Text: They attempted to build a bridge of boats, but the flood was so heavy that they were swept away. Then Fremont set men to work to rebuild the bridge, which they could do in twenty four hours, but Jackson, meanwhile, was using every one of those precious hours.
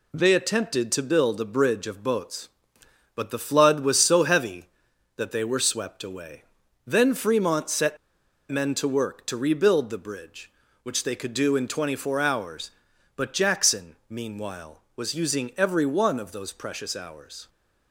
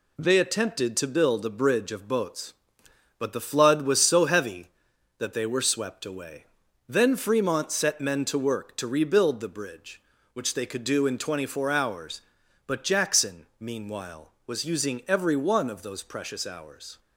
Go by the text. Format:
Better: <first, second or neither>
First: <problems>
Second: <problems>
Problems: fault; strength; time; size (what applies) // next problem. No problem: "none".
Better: second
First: pauses between "set" and "men"; noticeable; at 7.9 s; 0.51 s long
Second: none